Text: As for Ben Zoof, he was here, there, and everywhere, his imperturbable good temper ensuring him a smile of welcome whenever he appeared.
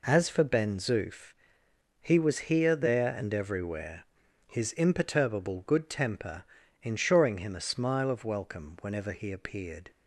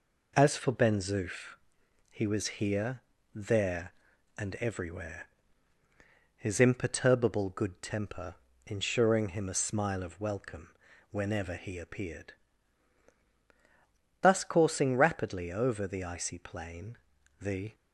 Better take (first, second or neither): first